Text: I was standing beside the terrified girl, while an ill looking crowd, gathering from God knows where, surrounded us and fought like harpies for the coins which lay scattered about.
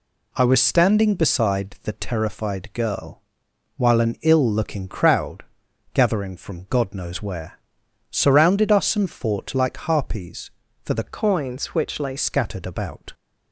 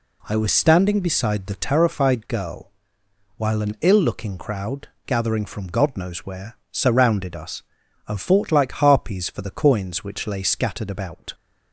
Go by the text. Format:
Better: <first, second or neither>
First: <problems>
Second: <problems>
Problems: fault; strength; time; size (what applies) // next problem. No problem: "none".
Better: second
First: changes voice from "coins" to "lay"; from 11.0 to 12.1 s; 1.1 s long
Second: none